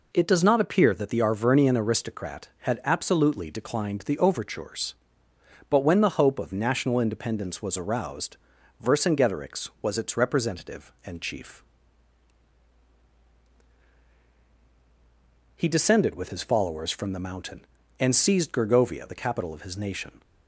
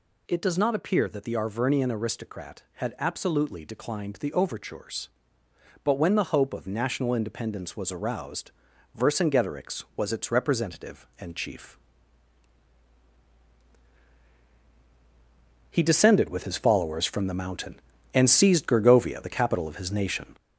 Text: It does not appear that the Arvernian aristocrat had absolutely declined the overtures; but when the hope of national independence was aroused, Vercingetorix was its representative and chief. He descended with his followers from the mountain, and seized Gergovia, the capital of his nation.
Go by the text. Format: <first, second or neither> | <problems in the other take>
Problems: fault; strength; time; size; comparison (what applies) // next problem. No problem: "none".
first | gets louder; noticeable; throughout; 4.5 dB